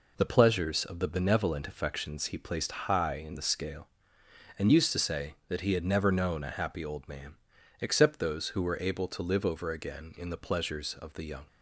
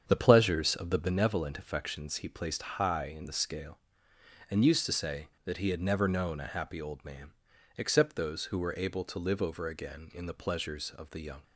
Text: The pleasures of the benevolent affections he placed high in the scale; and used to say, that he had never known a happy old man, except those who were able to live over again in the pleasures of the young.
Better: first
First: none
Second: starts louder than the rest; strong; until 1.2 s; 7.5 dB

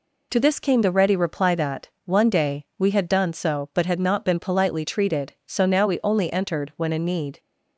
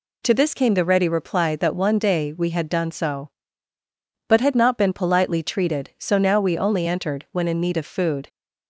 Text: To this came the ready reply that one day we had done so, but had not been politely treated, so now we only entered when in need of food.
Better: second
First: pauses between "that" and "one"; slight; at 1.8 s; 0.16 s long // stops before "of food"; at 7.4 s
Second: none

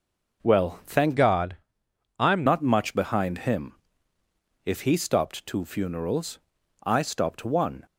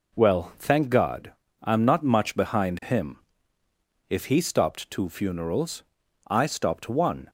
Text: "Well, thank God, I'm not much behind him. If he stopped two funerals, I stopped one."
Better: second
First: changes voice from "God" to "I'm"; from 1.1 to 2.4 s; 1.3 s long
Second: none

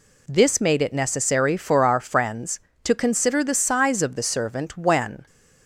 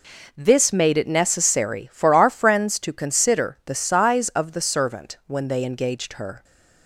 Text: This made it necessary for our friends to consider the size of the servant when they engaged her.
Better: second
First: stops before "they engaged her"; at 5.2 s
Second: none

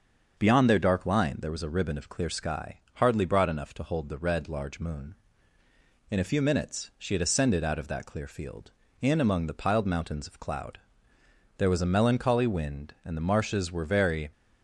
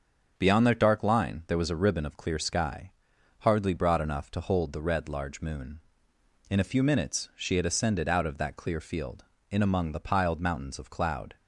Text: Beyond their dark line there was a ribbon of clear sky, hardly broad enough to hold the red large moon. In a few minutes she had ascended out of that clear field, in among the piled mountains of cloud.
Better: second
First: starts louder than the rest; until 1.4 s; 6.5 dB // goes on to say "There was a melancholy wind and the marshes were very"; strong; from 11.5 s on; 2.7 s long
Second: starts louder than the rest; until 1.3 s; 7 dB

